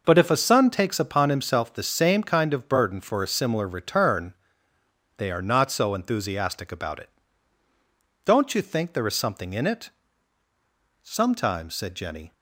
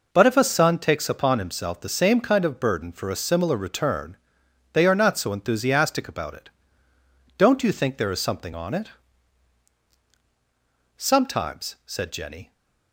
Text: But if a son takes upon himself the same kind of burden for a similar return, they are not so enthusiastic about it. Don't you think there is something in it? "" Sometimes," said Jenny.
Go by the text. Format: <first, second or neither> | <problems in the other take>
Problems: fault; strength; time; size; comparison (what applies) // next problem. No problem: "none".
first | says "on" for "in"; at 8.5 s